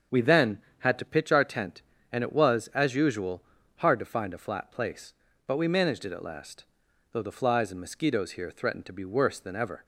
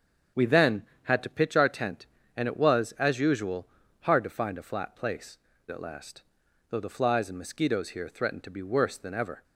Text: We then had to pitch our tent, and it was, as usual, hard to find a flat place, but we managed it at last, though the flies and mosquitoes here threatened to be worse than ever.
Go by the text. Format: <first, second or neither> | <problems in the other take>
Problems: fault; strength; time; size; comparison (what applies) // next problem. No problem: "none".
first | starts louder than the rest; strong; until 1.5 s; 7.5 dB; also in the first // skips "but we managed it"; at 5.5 s